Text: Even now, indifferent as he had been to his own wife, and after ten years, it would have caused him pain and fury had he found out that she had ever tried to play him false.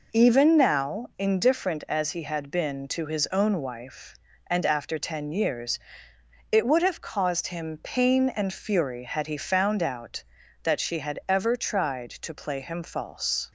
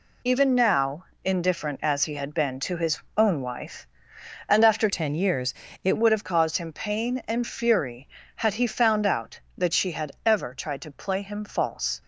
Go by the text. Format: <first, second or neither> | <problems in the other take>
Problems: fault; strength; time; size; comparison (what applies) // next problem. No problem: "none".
first | pauses between "his" and "own"; slight; at 2.9 s; 0.18 s long // changes voice from "ten" to "it"; from 4.9 to 5.9 s; 1.0 s long